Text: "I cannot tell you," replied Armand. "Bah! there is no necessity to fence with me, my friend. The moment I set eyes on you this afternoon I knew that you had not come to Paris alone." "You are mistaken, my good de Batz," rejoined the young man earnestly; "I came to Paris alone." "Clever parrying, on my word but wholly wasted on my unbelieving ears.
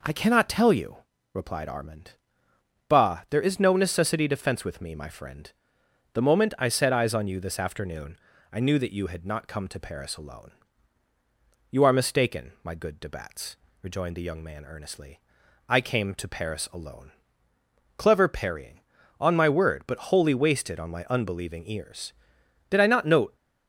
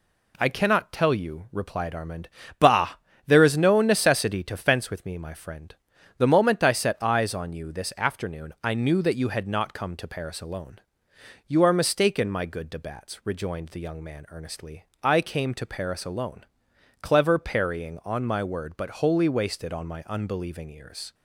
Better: second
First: pauses between "afternoon" and "I"; slight; at 8.1 s; 0.36 s long // goes on to say "Did I not note"; noticeable; from 22.6 s on; 0.68 s long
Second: none

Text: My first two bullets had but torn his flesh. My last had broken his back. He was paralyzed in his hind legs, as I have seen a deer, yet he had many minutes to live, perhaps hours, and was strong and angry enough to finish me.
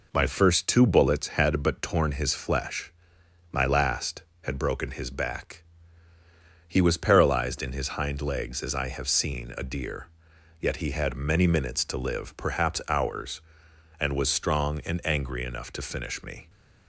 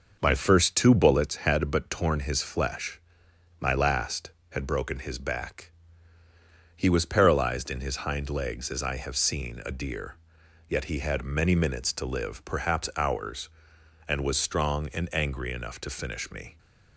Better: first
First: none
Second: starts louder than the rest; noticeable; until 1.3 s; 6 dB

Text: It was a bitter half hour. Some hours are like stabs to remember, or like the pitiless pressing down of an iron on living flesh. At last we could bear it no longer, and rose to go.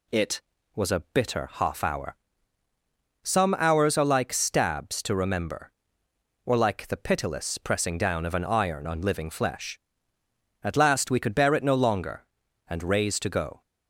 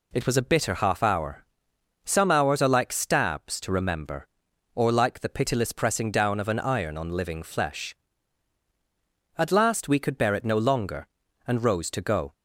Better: second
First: says "raise" for "rose"; at 12.8 s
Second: none

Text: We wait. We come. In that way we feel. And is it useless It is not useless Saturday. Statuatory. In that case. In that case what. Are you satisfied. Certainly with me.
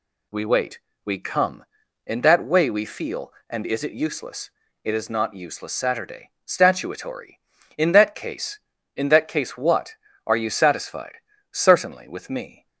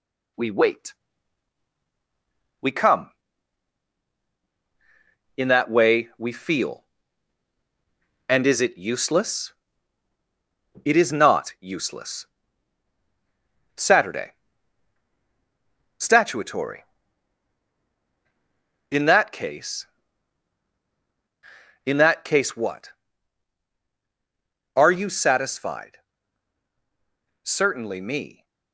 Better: first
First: pauses between "useless" and "It"; slight; at 4.5 s; 0.34 s long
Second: pauses between "useless" and "It"; strong; at 9.5 s; 1.3 s long // pauses between "useless" and "Saturday"; strong; at 12.2 s; 1.5 s long // skips "with"; at 27.9 s

